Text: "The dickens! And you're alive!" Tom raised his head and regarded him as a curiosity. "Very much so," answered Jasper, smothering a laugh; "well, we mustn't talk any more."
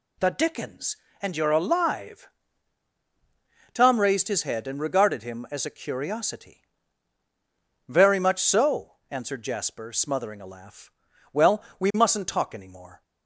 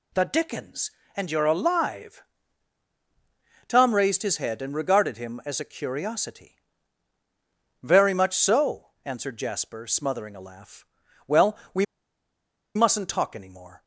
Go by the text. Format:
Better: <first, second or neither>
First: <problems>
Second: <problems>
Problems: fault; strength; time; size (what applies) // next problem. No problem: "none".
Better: first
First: none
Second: pauses between "we" and "mustn't"; noticeable; at 11.8 s; 0.90 s long